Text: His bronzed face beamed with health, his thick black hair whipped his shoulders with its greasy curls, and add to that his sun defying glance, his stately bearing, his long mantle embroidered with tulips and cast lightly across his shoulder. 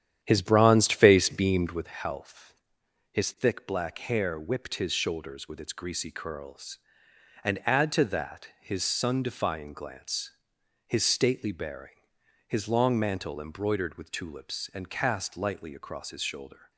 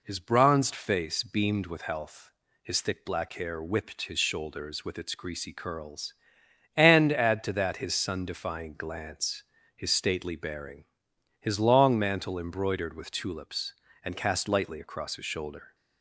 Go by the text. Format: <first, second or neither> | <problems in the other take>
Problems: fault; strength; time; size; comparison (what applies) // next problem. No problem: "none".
second | starts louder than the rest; strong; until 1.9 s; 10 dB